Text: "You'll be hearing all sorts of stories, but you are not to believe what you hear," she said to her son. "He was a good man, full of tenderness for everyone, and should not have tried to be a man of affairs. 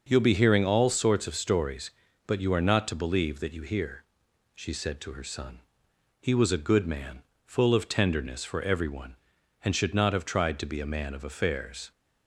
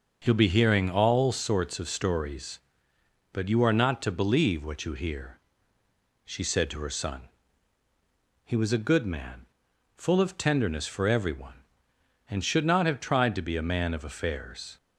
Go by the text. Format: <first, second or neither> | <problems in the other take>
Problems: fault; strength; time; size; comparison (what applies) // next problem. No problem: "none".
second | starts louder than the rest; until 1.1 s; 6 dB; also in the second // says "that" for "what"; at 3.4 s